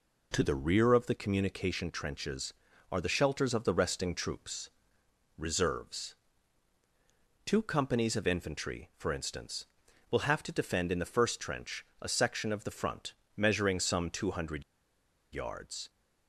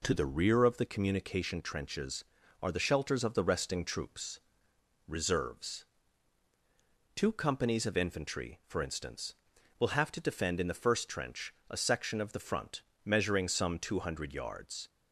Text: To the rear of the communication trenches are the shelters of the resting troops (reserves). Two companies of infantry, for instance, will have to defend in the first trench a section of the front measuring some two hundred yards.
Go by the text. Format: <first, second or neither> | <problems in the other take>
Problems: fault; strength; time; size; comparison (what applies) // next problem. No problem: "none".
second | pauses between "trench" and "a"; slight; at 11.8 s; 0.16 s long; slight in the second // pauses between "front" and "measuring"; slight; at 13.1 s; 0.24 s long; slight in the second // pauses between "hundred" and "yards"; noticeable; at 14.6 s; 0.70 s long